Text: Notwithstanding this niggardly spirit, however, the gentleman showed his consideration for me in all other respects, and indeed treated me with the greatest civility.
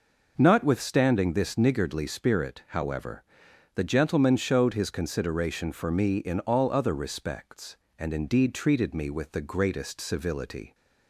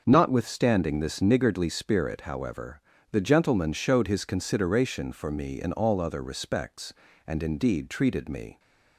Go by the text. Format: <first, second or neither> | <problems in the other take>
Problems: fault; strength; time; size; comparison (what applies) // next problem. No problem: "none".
first | starts louder than the rest; until 1.0 s; 6.5 dB // stops before "with the greatest civility"; at 8.5 s